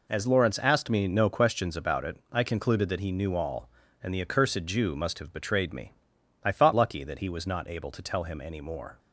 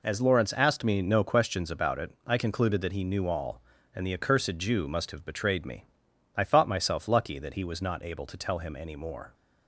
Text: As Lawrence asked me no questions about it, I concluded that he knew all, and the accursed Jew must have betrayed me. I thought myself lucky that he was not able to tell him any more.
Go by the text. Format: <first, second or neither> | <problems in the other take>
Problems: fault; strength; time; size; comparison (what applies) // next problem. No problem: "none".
second | skips "myself"; at 6.7 s